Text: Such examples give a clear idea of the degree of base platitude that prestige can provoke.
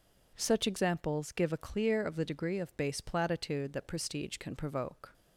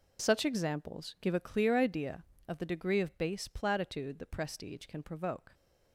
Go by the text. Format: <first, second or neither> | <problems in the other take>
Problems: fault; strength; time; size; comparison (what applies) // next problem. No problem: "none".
second | skips "idea"; at 2.0 s